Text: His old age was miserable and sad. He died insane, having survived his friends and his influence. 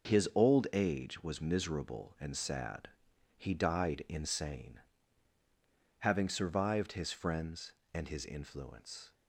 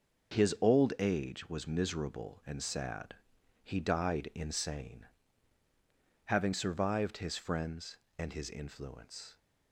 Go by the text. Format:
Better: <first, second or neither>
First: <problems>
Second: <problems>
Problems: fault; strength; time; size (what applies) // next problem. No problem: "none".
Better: neither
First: starts louder than the rest; noticeable; until 1.1 s; 6 dB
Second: starts louder than the rest; until 1.4 s; 6 dB